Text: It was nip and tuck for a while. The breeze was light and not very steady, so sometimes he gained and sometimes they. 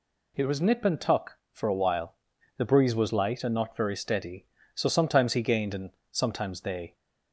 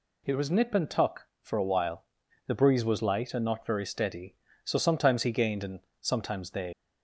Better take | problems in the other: first | pauses between "and" and "sometimes"; slight; at 5.7 s; 0.20 s long; slight in the first // leaves "they" unfinished; at 6.7 s; 110 ms

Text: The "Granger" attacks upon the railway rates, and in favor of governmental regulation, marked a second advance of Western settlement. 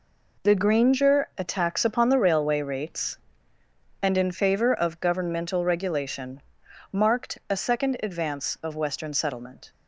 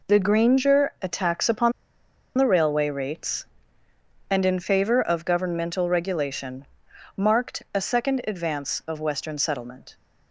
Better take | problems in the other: first | pauses between "upon" and "the"; noticeable; at 1.7 s; 0.66 s long

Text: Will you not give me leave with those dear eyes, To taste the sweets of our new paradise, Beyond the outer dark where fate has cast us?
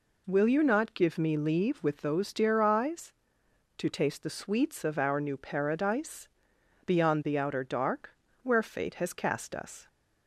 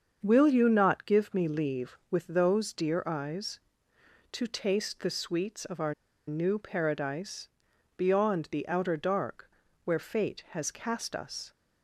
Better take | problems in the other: first | starts louder than the rest; until 1.2 s; 7 dB // pauses between "our" and "new"; slight; at 5.9 s; 0.34 s long // pauses between "dark" and "where"; slight; at 9.5 s; 0.34 s long; slight in the first

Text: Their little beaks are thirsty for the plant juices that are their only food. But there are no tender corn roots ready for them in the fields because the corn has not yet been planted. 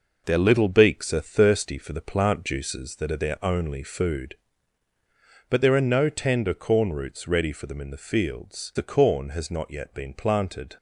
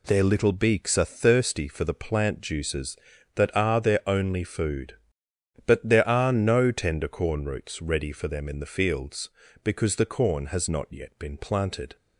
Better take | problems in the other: second | skips "because"; at 8.7 s

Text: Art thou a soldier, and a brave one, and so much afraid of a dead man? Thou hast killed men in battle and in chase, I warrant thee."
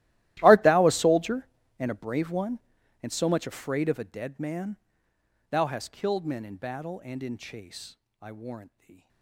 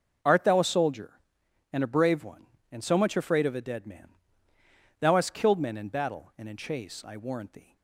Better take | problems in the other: second | gets quieter; strong; throughout; 22 dB

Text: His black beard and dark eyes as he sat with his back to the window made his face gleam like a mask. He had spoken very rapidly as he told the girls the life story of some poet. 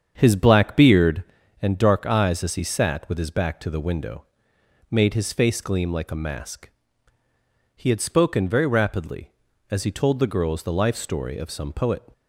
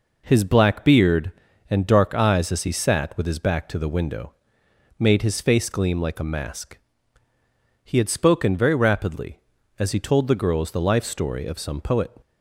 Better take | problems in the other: second | starts louder than the rest; strong; until 1.5 s; 7.5 dB // pauses between "window" and "made"; noticeable; at 4.2 s; 0.66 s long; noticeable in the second

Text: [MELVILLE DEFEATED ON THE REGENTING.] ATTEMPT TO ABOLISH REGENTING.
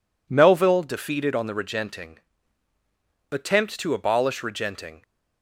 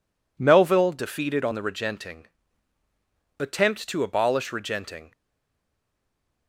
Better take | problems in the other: first | stays silent after the last word; noticeable; from 5.1 s on; 1.3 s long

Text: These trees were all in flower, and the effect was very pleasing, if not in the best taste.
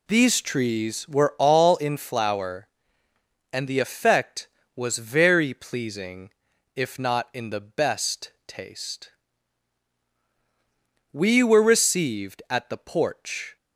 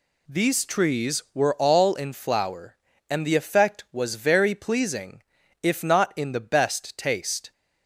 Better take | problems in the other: second | pauses between "best" and "taste"; slight; at 8.3 s; 0.16 s long // goes on to say "We were received at the porch"; strong; from 11.1 s on; 2.4 s long

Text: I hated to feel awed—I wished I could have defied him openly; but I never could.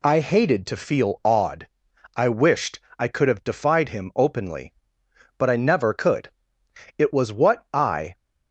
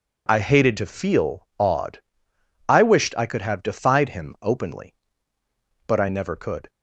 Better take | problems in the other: second | pauses between "wished" and "I"; slight; at 2.8 s; 0.18 s long // goes on to say "It was what I"; noticeable; from 6.9 s on; 1.1 s long

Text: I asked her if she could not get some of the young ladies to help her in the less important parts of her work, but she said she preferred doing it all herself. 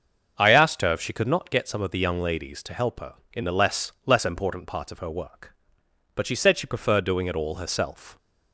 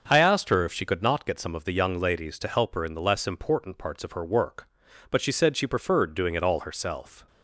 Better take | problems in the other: second | starts louder than the rest; until 1.3 s; 6.5 dB; also in the second // says "less" twice; at 4.0 s

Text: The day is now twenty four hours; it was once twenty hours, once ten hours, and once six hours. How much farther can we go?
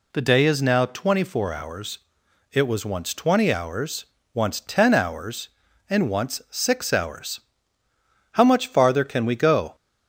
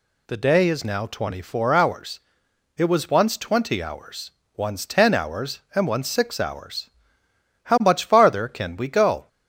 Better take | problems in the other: neither | none

